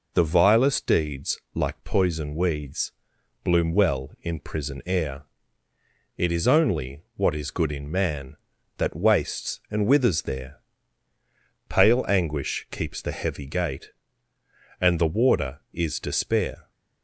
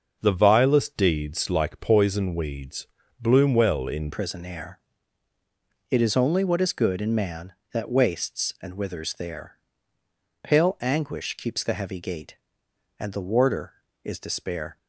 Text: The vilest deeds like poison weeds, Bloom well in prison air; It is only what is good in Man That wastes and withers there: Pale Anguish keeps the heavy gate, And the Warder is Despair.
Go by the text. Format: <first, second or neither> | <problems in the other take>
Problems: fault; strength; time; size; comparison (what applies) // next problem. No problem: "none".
first | starts louder than the rest; until 1.2 s; 6 dB // changes voice at "prison"; from 4.1 s on; 10.6 s long